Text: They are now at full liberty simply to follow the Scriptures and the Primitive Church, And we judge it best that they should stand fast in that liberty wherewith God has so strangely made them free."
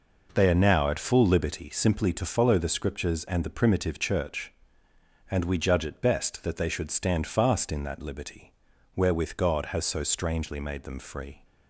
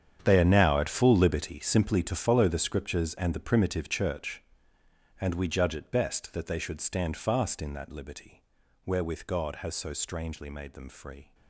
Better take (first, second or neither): first